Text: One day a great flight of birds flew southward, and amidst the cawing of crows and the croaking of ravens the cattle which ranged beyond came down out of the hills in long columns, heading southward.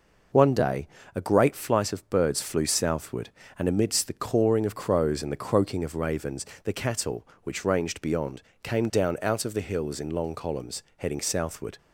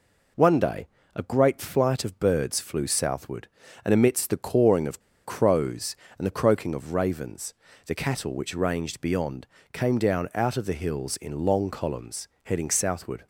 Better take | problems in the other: first | pauses between "day" and "a"; slight; at 0.8 s; 0.26 s long; slight in the first // pauses between "of" and "crows"; slight; at 5.0 s; 0.25 s long // pauses between "ravens" and "the"; slight; at 7.5 s; 0.32 s long; slight in the first // pauses between "beyond" and "came"; slight; at 9.4 s; 0.28 s long; slight in the first

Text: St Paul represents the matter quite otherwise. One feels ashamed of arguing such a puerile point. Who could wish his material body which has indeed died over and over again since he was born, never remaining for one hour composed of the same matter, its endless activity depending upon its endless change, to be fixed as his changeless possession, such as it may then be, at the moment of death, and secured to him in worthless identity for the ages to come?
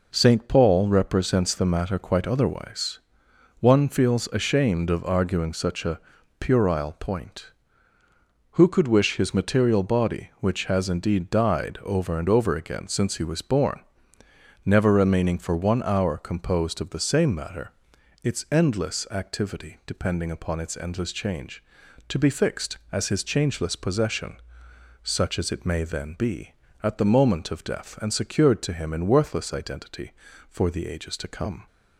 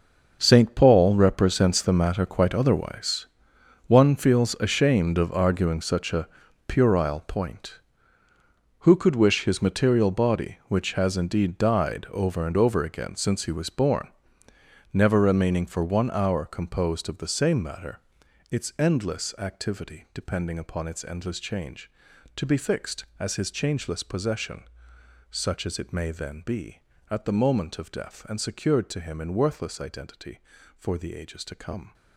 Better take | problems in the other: first | gets quieter; strong; throughout; 14 dB // pauses between "a" and "puerile"; at 6.2 s; 0.40 s long; also in the first

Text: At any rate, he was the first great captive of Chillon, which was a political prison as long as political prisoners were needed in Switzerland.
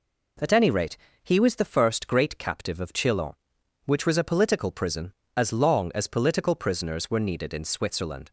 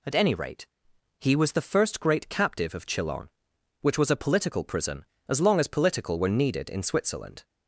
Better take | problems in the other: first | skips "prisoners"; at 6.1 s

